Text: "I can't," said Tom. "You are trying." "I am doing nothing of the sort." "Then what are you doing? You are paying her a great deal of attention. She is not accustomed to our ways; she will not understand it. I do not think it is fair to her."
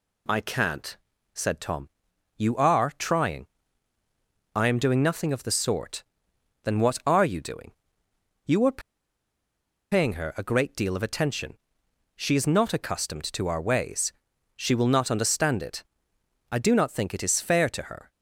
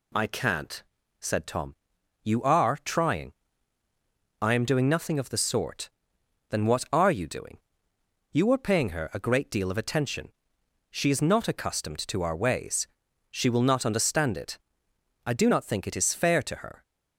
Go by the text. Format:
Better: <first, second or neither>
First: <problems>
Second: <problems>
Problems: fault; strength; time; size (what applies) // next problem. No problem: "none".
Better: second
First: pauses between "are" and "paying"; at 8.8 s; 1.1 s long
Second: none